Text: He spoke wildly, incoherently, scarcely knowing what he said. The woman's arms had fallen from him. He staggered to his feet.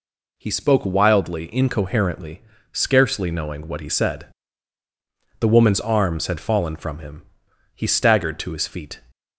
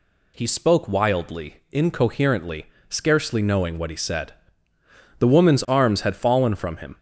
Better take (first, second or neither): first